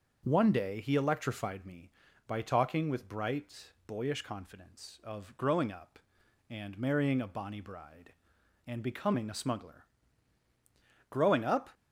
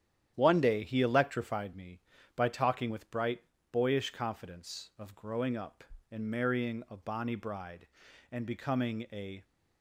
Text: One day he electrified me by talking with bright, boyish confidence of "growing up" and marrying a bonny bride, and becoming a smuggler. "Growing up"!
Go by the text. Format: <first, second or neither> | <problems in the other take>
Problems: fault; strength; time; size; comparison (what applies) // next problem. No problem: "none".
first | starts louder than the rest; strong; until 1.3 s; 10 dB; also in the first // stops before "smuggler Growing up"; at 9.4 s